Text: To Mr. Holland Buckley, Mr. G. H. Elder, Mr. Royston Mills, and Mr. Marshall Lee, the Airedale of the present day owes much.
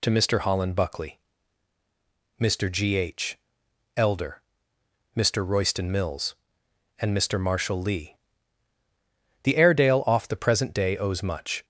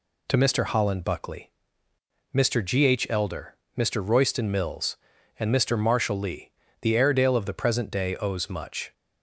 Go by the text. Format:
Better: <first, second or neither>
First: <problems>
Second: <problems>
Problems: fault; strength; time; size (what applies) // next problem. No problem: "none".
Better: second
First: pauses between "H" and "Elder"; noticeable; at 3.3 s; 0.60 s long // says "off" for "of"; at 10.0 s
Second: none